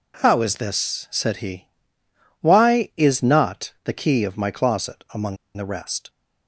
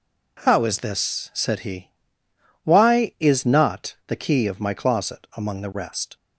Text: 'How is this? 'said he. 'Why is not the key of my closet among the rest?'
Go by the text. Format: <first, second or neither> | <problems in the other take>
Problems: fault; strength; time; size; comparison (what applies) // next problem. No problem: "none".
second | pauses between "among" and "the"; slight; at 5.3 s; 0.20 s long